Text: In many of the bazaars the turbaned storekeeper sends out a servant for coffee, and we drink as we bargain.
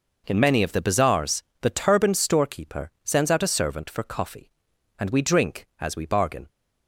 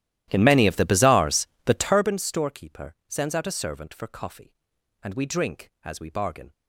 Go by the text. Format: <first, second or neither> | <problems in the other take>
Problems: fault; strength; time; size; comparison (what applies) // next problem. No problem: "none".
first | starts louder than the rest; strong; until 2.2 s; 13.5 dB // pauses between "bazaars" and "the"; slight; at 1.4 s; 0.18 s long; slight in the first